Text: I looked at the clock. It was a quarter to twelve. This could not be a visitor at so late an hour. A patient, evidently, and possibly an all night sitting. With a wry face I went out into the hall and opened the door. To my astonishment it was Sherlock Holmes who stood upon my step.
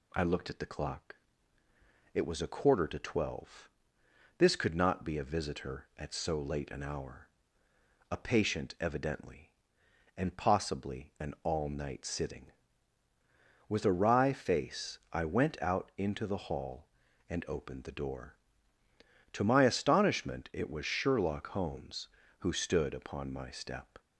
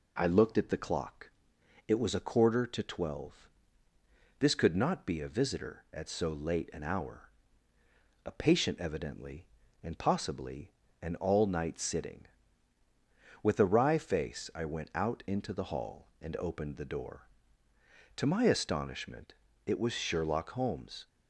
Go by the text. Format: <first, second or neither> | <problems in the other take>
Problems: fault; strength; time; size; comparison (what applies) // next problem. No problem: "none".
first | pauses between "possibly" and "an"; slight; at 10.7 s; 0.32 s long // pauses between "astonishment" and "it"; slight; at 19.3 s; 0.32 s long // stops before "who stood upon my step"; at 21.0 s